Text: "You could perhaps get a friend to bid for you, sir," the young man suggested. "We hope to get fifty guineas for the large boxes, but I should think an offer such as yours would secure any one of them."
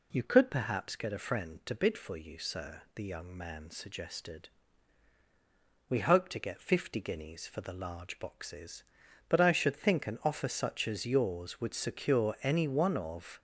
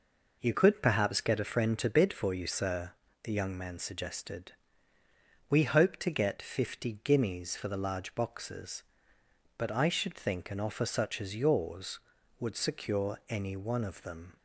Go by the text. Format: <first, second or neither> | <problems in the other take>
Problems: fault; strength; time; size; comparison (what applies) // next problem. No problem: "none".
second | stops before "them"; at 13.3 s